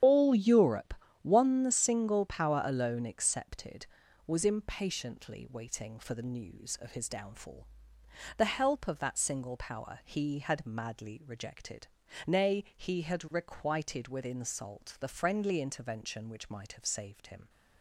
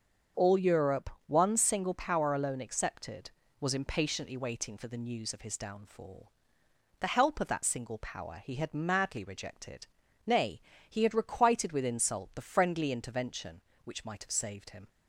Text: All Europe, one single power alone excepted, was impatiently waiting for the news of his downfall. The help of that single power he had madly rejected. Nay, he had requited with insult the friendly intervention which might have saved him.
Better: second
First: loses the start of "All"; at 0.0 s; 50 ms // starts louder than the rest; strong; until 1.3 s; 9 dB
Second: starts louder than the rest; until 1.5 s; 6.5 dB

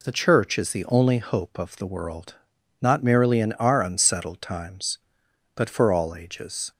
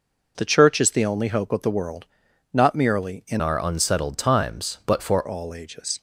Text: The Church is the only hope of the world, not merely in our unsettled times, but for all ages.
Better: first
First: none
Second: changes voice from "our" to "for"; from 3.4 to 5.2 s; 1.8 s long

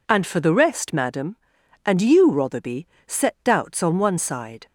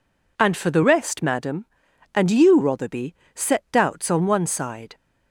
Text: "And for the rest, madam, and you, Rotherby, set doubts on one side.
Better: neither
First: none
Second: none

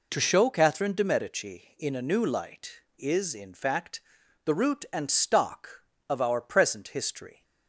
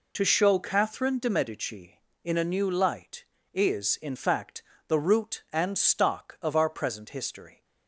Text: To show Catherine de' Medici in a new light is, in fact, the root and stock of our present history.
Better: neither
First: none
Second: none

